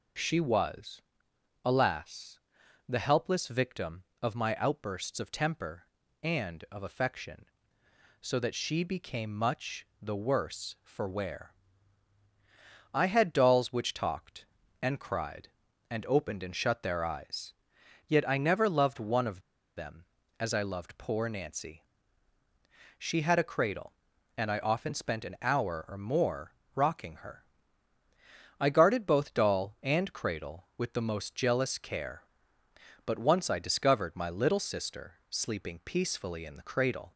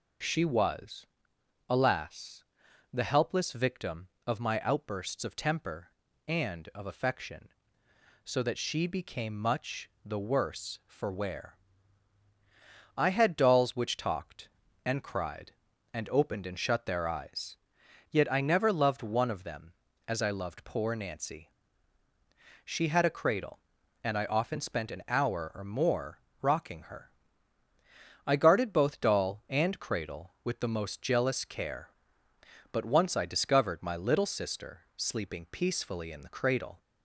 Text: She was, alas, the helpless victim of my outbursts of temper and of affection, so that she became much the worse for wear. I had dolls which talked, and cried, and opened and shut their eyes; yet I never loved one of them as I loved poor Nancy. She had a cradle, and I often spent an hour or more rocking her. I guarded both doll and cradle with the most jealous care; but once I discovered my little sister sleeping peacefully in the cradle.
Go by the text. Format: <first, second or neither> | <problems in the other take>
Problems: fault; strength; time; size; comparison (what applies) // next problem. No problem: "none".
second | pauses between "much" and "the"; slight; at 9.8 s; 0.16 s long; slight in the second // pauses between "of" and "them"; slight; at 19.4 s; 0.35 s long // pauses between "more" and "rocking"; slight; at 26.5 s; 0.24 s long; slight in the second // pauses between "sister" and "sleeping"; slight; at 35.1 s; 0.16 s long; slight in the second